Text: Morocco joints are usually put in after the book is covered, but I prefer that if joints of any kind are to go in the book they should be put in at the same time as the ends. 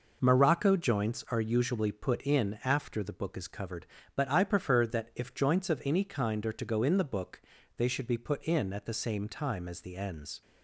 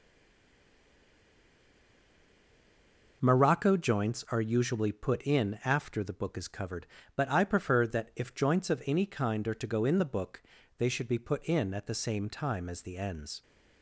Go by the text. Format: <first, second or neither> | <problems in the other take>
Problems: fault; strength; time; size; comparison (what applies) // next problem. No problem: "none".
first | stays silent before the first word; strong; until 3.2 s; 3.2 s long // pauses between "book" and "they"; slight; at 10.4 s; 0.36 s long; slight in the first